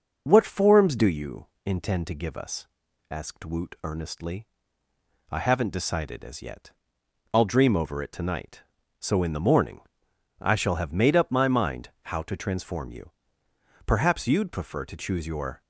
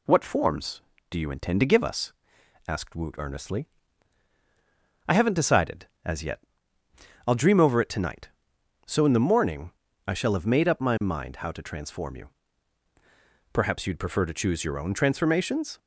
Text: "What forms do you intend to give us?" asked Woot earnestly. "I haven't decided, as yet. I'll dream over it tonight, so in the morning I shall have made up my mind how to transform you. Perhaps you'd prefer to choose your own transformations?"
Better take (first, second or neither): second